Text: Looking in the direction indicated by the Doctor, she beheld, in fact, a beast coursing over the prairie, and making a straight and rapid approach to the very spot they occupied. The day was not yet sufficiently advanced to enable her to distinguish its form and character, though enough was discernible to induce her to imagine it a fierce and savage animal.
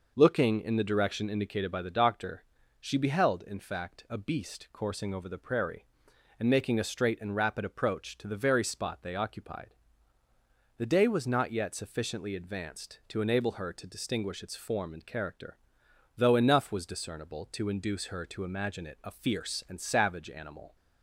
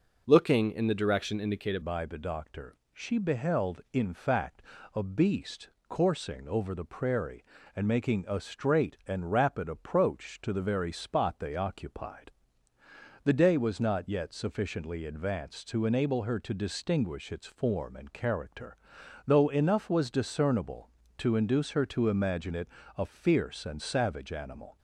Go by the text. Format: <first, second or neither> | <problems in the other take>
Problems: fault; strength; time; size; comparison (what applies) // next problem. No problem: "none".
first | changes voice at "by"; from 1.8 s on; 22.9 s long // pauses between "beast" and "coursing"; slight; at 5.6 s; 0.22 s long // pauses between "it" and "a"; slight; at 22.6 s; 0.26 s long